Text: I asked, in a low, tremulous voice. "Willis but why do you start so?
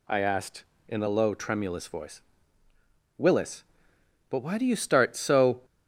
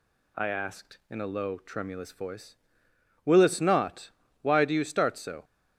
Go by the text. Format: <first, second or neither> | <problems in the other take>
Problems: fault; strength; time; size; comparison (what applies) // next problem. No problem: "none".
first | says "not" for "but"; at 3.5 s